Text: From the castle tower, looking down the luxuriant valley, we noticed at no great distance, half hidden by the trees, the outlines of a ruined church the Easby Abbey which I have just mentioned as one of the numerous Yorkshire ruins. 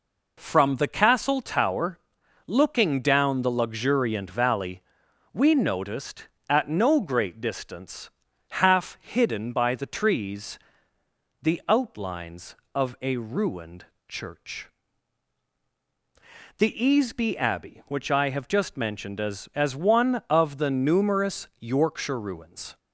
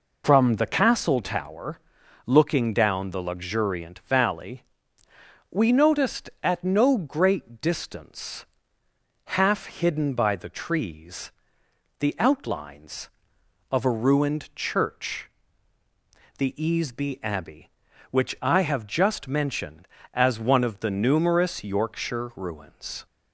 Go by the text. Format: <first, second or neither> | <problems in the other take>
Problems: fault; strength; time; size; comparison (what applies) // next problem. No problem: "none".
second | pauses between "ruined" and "church"; slight; at 13.8 s; 0.22 s long // pauses between "church" and "the"; strong; at 14.6 s; 1.8 s long; also in the second // says "as" twice; at 19.5 s